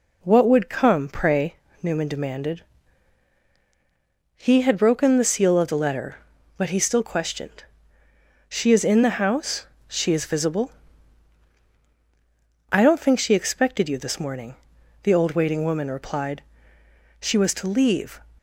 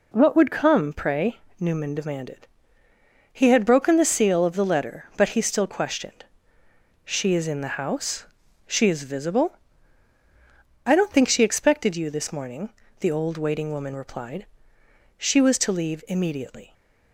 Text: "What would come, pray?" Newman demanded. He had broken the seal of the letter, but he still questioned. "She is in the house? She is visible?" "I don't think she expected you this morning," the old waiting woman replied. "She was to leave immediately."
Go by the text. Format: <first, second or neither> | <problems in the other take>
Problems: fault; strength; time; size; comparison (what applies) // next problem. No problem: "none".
second | stops before "immediately"; at 18.3 s